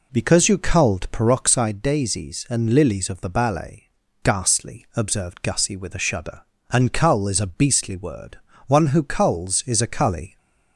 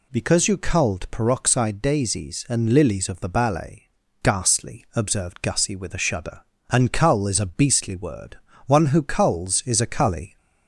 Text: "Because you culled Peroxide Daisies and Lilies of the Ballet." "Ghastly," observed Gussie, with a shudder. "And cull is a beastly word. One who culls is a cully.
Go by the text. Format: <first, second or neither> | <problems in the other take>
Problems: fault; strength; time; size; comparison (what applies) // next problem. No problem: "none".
second | starts louder than the rest; noticeable; until 1.7 s; 4 dB